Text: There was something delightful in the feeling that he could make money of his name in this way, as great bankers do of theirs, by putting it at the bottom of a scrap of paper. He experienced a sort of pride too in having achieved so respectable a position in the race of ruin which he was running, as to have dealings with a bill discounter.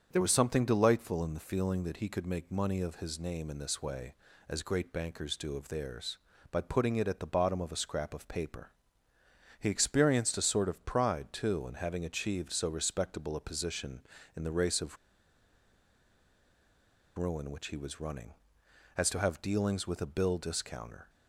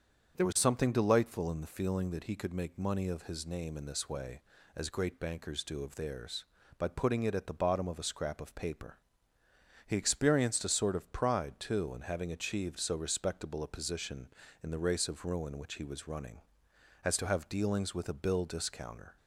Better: second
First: starts louder than the rest; strong; until 1.1 s; 7.5 dB // pauses between "of" and "ruin"; strong; at 14.9 s; 2.2 s long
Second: starts louder than the rest; until 1.4 s; 7 dB

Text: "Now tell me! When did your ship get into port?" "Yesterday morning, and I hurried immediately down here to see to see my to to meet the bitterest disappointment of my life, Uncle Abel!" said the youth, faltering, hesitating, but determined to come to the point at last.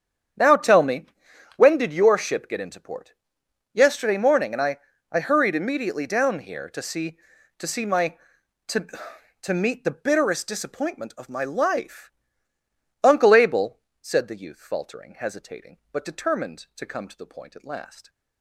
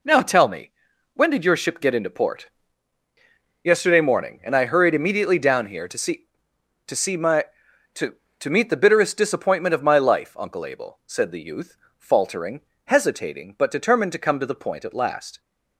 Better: second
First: starts louder than the rest; strong; until 1.8 s; 8.5 dB // says "I" twice; at 5.0 s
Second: none

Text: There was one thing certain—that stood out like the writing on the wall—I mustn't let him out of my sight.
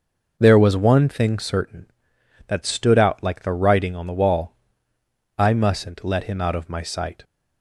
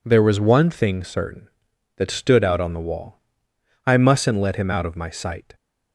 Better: first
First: none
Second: skips "like the writing"; at 2.5 s

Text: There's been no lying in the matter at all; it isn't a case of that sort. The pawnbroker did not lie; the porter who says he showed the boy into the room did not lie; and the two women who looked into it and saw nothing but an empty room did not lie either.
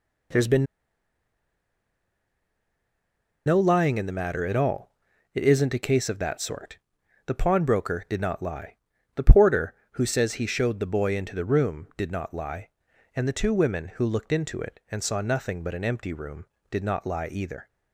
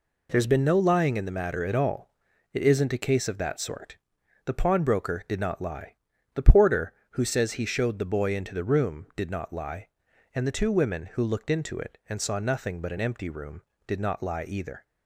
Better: second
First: pauses between "been" and "no"; strong; at 0.6 s; 2.8 s long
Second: none

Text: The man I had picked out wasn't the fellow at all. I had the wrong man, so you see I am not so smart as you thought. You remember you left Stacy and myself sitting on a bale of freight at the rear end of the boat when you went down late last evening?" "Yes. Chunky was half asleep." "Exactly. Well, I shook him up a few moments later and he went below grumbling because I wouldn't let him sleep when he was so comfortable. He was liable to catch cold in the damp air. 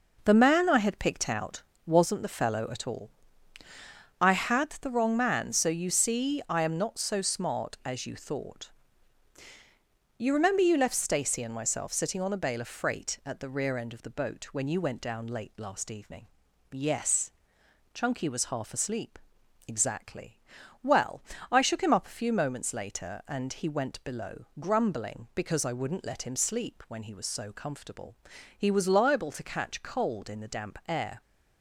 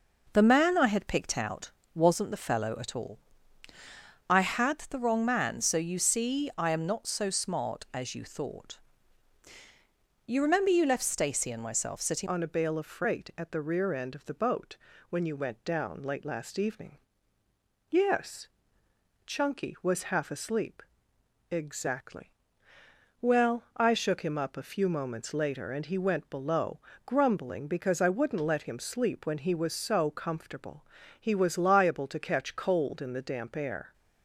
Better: first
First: pauses between "out" and "wasn't"; slight; at 1.6 s; 0.24 s long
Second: pauses between "out" and "wasn't"; slight; at 1.6 s; 0.24 s long // changes voice at "on"; from 12.2 s on; 21.7 s long // pauses between "boat" and "when"; slight; at 14.7 s; 0.32 s long // pauses between "below" and "grumbling"; slight; at 26.7 s; 0.26 s long

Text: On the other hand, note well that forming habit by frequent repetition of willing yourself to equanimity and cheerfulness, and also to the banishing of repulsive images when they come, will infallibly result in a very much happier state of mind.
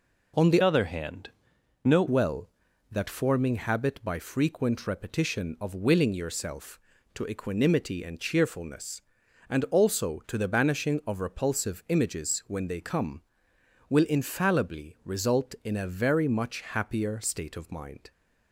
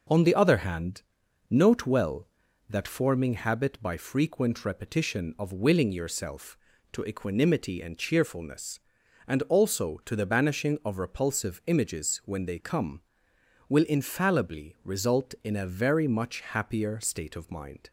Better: second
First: changes voice from "other" to "note"; from 0.6 to 2.0 s; 1.4 s long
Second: none

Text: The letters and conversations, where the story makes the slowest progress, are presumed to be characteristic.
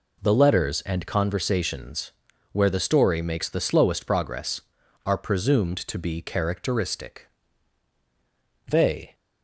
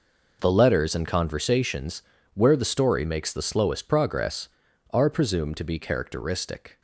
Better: second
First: goes on to say "They"; slight; from 8.6 s on; 0.46 s long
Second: none

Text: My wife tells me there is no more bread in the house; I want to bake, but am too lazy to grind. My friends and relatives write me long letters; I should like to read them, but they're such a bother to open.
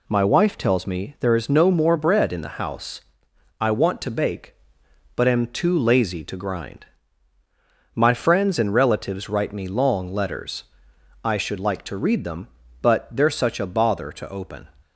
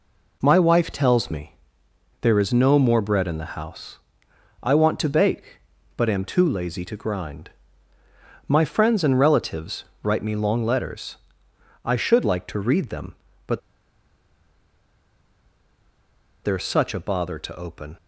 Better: first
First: none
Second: pauses between "me" and "there"; noticeable; at 1.5 s; 0.64 s long // pauses between "relatives" and "write"; slight; at 9.8 s; 0.22 s long // pauses between "but" and "they're"; strong; at 13.5 s; 2.8 s long

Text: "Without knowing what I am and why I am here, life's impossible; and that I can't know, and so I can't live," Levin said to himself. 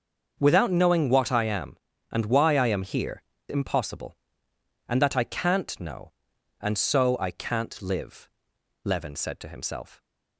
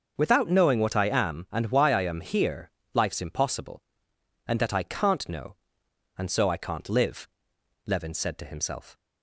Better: second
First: starts louder than the rest; until 1.4 s; 6.5 dB // skips "life's"; at 3.3 s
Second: starts louder than the rest; until 1.1 s; 6.5 dB

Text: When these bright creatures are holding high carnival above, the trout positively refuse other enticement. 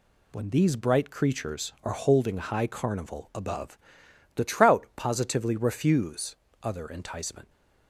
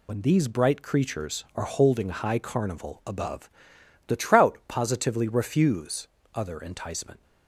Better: first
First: pauses between "refuse" and "other"; slight; at 6.3 s; 0.26 s long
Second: loses the start of "When"; at 0.0 s; 55 ms // pauses between "refuse" and "other"; slight; at 6.0 s; 0.26 s long

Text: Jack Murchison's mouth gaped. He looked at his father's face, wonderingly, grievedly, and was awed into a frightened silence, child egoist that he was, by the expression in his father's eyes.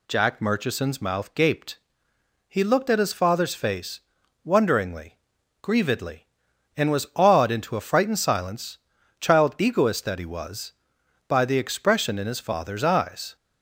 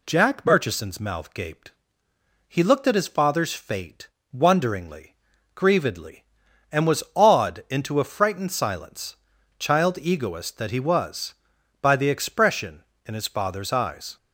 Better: first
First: none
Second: says "fate" for "face"; at 3.5 s

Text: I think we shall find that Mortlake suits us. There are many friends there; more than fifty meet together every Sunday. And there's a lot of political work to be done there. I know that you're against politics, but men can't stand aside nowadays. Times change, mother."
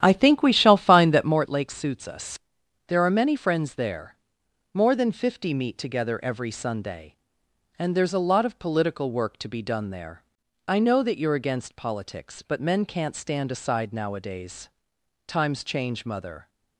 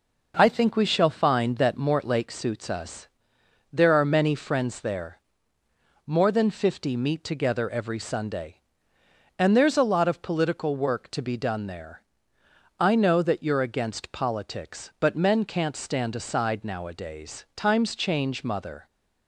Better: second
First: starts louder than the rest; strong; until 1.4 s; 10.5 dB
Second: none

